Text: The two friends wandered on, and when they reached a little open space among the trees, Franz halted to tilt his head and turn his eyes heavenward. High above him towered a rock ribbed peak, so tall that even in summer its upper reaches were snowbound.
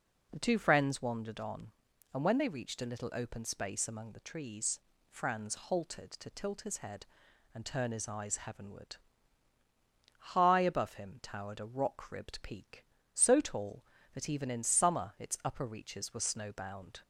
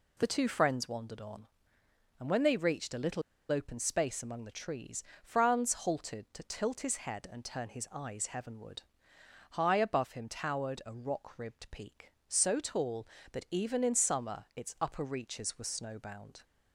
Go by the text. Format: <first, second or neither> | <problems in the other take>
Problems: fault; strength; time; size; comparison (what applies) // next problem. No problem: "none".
first | pauses between "little" and "open"; slight; at 3.2 s; 0.29 s long